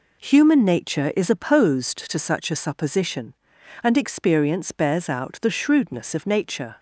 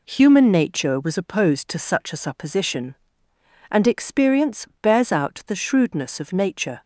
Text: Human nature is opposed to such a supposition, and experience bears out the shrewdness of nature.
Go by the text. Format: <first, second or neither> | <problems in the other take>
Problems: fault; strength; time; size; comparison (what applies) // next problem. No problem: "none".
first | says "was" for "is"; at 0.9 s // pauses between "experience" and "bears"; slight; at 4.6 s; 0.16 s long